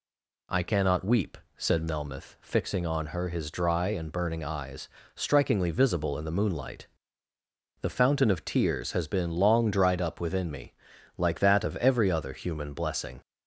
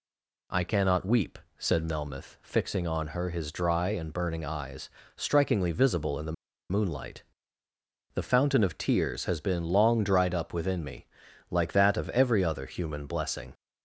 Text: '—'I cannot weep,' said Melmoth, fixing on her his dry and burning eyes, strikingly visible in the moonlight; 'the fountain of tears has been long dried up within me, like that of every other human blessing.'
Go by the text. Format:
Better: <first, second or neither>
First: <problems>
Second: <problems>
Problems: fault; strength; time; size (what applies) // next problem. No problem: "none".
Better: first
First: none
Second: stays silent before the first word; slight; until 0.5 s; 0.5 s long // pauses between "the" and "moonlight"; at 6.3 s; 0.37 s long